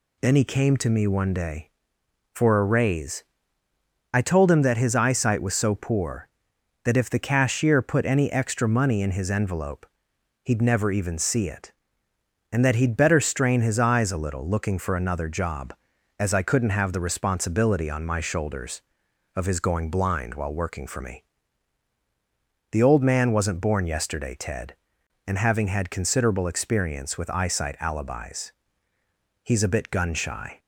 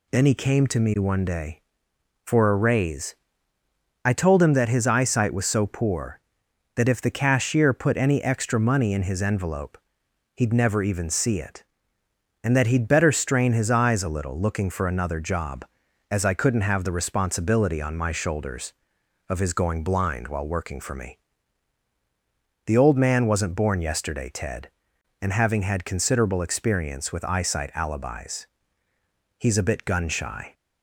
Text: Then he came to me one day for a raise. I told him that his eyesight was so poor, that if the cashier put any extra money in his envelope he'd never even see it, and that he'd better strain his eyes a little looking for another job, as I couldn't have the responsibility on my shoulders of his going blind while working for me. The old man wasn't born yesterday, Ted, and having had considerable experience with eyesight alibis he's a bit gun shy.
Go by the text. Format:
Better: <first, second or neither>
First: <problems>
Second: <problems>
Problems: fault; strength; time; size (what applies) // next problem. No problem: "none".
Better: neither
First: pauses between "envelope" and "he'd"; noticeable; at 9.8 s; 0.58 s long // pauses between "alibis" and "he's"; noticeable; at 28.5 s; 0.90 s long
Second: pauses between "envelope" and "he'd"; noticeable; at 9.7 s; 0.58 s long // pauses between "alibis" and "he's"; noticeable; at 28.4 s; 0.90 s long